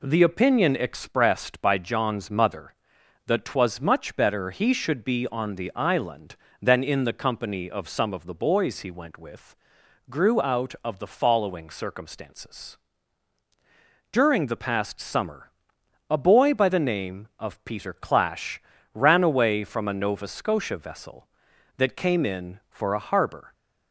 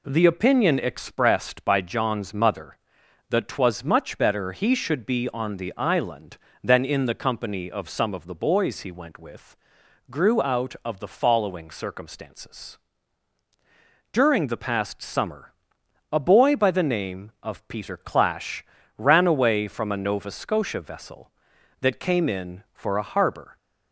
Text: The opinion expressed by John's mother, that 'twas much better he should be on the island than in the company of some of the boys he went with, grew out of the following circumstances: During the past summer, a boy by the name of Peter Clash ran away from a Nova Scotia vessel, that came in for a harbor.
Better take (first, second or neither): neither